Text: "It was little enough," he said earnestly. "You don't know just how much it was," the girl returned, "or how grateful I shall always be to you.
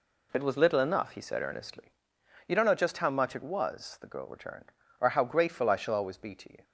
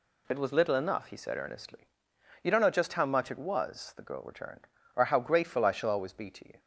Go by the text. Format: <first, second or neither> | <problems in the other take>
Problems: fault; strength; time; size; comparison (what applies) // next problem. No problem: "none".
second | starts louder than the rest; slight; until 2.0 s; 2.5 dB